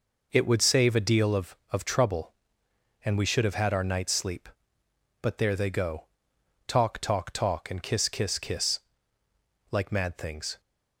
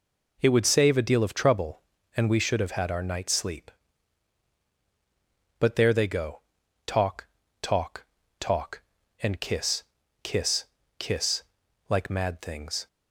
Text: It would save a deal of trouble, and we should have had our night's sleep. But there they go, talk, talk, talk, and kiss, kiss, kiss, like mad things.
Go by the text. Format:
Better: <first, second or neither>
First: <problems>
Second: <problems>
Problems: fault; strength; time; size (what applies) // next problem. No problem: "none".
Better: second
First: says "of" twice; at 1.7 s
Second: none